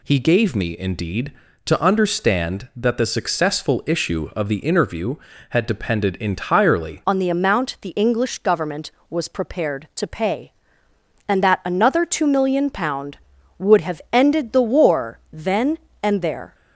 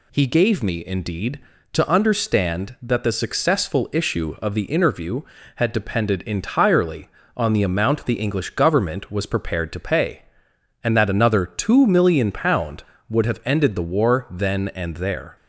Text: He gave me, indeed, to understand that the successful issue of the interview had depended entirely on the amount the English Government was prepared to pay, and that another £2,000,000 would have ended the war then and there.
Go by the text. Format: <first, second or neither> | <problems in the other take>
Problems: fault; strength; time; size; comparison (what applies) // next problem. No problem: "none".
second | changes voice at "on"; from 7.0 s on; 9.5 s long